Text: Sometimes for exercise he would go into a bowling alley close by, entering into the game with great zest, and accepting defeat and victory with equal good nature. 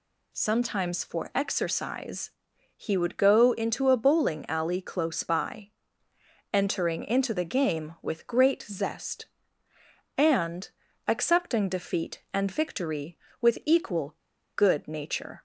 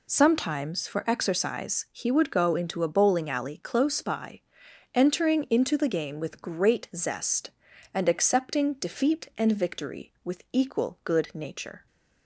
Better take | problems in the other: second | pauses between "exercise" and "he"; at 2.3 s; 0.44 s long // pauses between "and" and "accepting"; at 10.6 s; 0.38 s long // pauses between "equal" and "good"; at 14.1 s; 0.40 s long

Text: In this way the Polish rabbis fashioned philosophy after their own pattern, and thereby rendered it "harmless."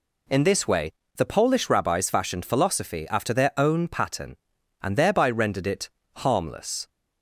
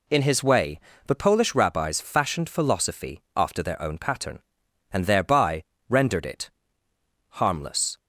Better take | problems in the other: first | says "his" for "this"; at 0.2 s // pauses between "way" and "the"; slight; at 0.7 s; 0.28 s long; slight in the first // pauses between "thereby" and "rendered"; slight; at 5.6 s; 0.26 s long // pauses between "it" and "harmless"; noticeable; at 6.4 s; 0.90 s long; slight in the first

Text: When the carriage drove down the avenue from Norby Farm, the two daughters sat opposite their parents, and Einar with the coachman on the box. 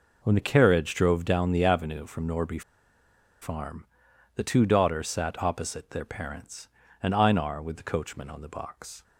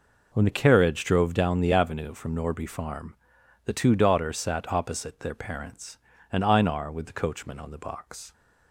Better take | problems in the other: second | pauses between "Norby" and "Farm"; noticeable; at 2.6 s; 0.80 s long

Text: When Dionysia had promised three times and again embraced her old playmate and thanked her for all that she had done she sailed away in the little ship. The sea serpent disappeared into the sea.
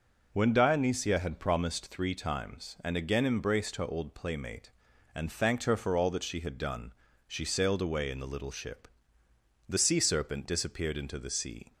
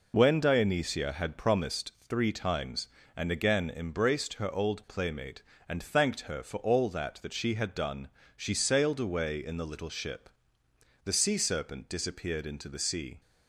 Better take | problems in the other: first | says "that" twice; at 7.2 s // pauses between "done" and "she"; slight; at 8.0 s; 0.28 s long; slight in the first

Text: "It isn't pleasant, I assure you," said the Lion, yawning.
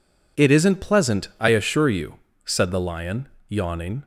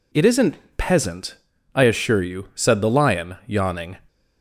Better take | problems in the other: first | says "peasant" for "pleasant"; at 0.7 s

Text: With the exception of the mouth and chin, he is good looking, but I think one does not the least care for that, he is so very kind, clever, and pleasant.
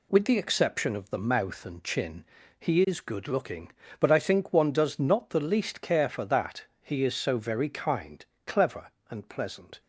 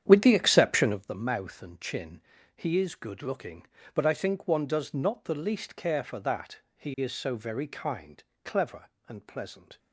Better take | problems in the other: first | starts louder than the rest; strong; until 1.1 s; 9.5 dB

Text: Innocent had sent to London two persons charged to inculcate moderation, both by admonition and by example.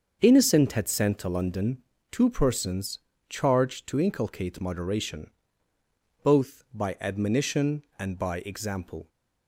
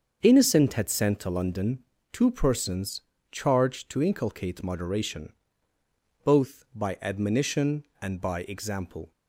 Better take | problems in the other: neither | starts louder than the rest; the same in both // pauses between "London" and "two"; slight; the same in both // pauses between "persons" and "charged"; slight; the same in both

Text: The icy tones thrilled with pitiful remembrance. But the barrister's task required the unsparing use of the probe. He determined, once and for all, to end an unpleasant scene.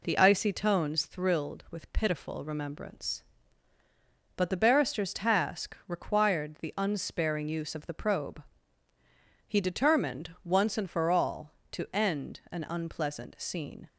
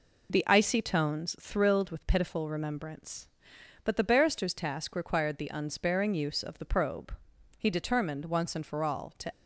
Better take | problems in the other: first | stops before "end an unpleasant scene"; at 9.3 s

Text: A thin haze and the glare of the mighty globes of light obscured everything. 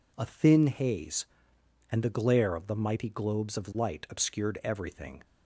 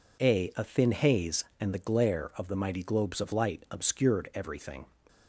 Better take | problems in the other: first | says "A" twice; at 0.5 s

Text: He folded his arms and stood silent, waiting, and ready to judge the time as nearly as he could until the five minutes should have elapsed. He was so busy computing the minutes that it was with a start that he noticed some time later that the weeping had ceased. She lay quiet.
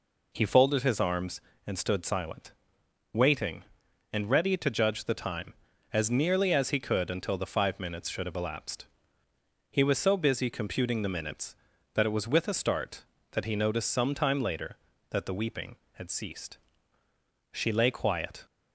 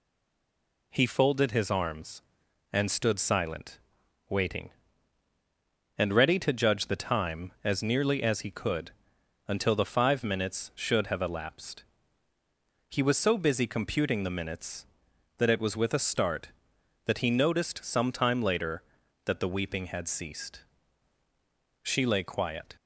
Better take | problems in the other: first | stays silent before the first word; slight; until 0.9 s; 0.9 s long // pauses between "could" and "until"; noticeable; at 8.9 s; 0.56 s long

